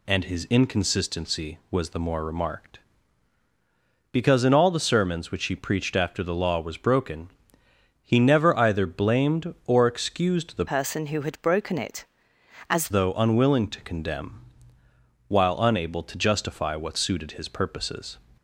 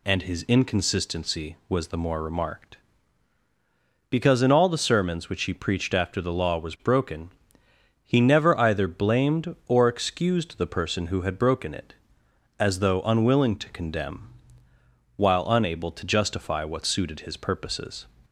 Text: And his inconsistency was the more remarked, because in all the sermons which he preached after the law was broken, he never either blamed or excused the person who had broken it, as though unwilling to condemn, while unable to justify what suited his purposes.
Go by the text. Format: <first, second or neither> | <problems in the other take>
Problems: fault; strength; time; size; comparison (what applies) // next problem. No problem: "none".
second | changes voice from "person" to "as"; from 10.6 to 12.8 s; 2.2 s long